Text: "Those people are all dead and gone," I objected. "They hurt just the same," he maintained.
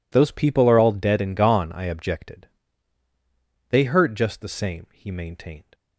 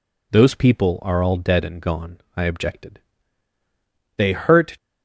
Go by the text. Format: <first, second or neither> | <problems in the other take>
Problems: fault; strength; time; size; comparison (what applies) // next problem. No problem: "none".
first | stops before "just the same he maintained"; at 4.7 s